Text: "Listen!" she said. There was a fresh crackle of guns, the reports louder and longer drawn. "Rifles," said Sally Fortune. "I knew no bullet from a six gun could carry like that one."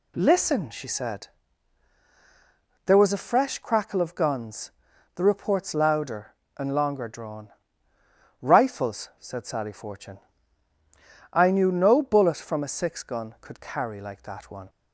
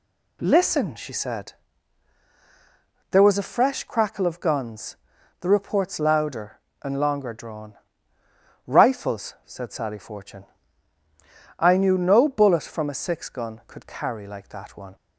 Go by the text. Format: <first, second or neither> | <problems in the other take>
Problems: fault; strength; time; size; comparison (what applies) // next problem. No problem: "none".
neither | none